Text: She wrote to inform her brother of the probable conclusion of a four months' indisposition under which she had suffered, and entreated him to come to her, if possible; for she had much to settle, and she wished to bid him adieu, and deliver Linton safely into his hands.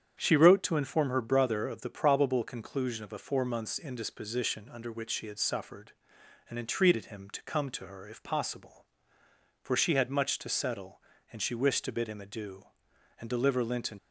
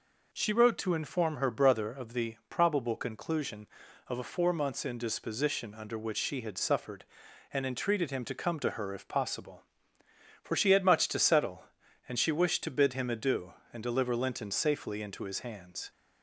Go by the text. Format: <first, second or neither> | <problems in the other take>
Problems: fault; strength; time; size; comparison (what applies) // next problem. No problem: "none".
second | starts louder than the rest; strong; until 1.1 s; 8.5 dB // stops before "safely into his hands"; at 13.9 s